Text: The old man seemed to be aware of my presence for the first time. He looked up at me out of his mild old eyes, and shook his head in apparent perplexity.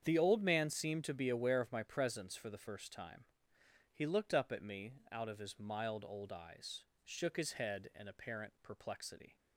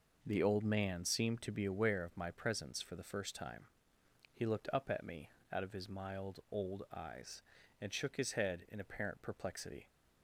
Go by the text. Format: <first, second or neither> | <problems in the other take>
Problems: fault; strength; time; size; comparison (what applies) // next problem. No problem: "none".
second | starts louder than the rest; strong; until 1.0 s; 8 dB // pauses between "me" and "out"; slight; at 4.9 s; 0.16 s long; slight in the second // skips "and"; at 6.9 s